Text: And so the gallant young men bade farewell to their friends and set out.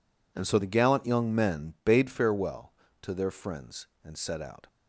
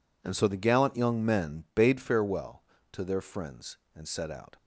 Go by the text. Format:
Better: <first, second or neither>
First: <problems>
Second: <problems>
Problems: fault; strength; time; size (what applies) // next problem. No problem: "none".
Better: neither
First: none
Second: none